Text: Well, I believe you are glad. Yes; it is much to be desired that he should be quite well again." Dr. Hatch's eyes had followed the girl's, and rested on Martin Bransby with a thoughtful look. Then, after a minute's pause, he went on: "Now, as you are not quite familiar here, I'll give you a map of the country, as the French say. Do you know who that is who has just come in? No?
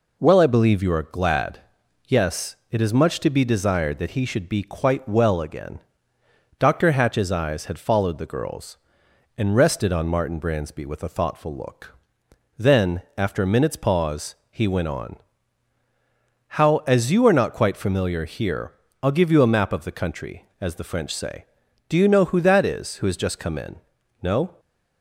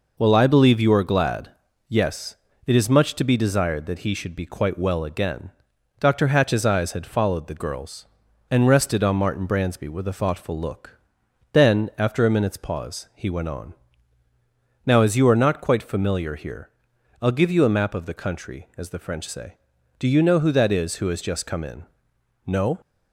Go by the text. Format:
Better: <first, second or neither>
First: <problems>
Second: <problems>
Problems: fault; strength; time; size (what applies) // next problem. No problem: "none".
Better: second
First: says "How" for "Now"; at 16.5 s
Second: none